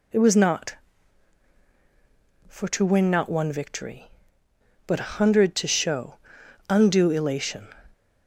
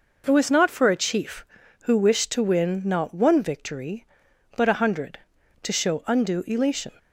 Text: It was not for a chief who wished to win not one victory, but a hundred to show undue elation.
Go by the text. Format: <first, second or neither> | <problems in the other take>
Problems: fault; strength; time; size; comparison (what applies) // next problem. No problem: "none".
second | skips "a chief who wished"; at 2.6 s // pauses between "show" and "undue"; noticeable; at 6.1 s; 0.54 s long